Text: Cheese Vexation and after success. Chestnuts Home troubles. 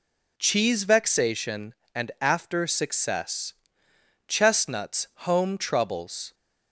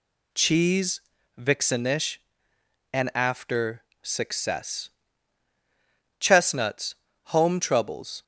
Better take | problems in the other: first | says "Vixenish" for "Vexation"; at 1.3 s // pauses between "after" and "success"; slight; at 3.8 s; 0.20 s long // pauses between "Chestnuts" and "Home"; slight; at 6.9 s; 0.30 s long

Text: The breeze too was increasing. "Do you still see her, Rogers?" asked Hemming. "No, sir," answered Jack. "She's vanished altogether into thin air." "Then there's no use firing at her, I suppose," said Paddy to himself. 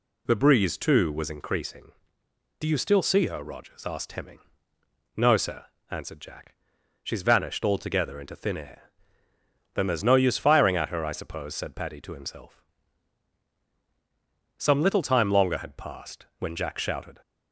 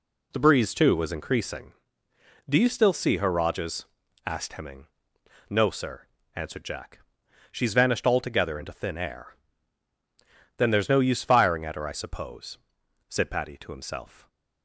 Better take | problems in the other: second | goes on to say "Some little time longer had passed when Jack shouted"; strong; from 14.5 s on; 2.6 s long

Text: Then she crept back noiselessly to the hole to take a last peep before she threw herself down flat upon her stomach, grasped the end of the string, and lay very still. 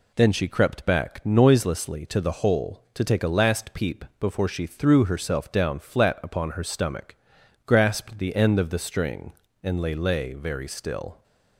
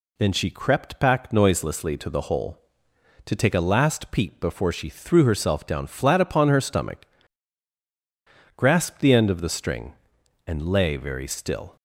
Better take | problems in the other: second | says "lay" twice; at 9.9 s

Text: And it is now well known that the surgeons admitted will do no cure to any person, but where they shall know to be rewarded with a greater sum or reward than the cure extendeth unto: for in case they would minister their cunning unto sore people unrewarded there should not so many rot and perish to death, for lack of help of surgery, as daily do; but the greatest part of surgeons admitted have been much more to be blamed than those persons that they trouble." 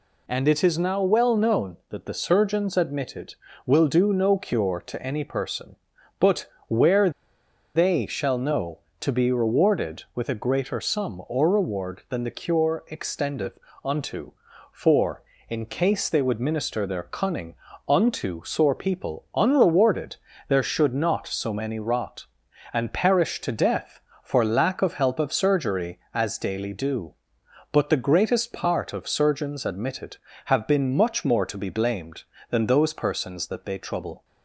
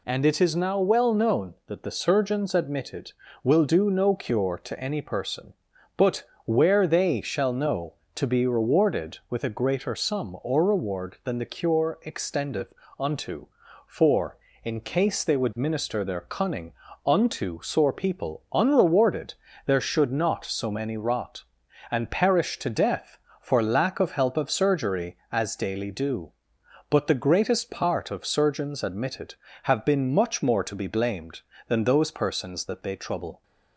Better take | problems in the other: second | pauses between "but" and "where"; slight; at 6.4 s; 0.22 s long; slight in the second // pauses between "where" and "they"; noticeable; at 7.0 s; 0.65 s long // pauses between "extendeth" and "unto"; slight; at 13.5 s; 0.26 s long; slight in the second // pauses between "cunning" and "unto"; slight; at 17.5 s; 0.34 s long; slight in the second // pauses between "unrewarded" and "there"; slight; at 20.1 s; 0.32 s long; slight in the second

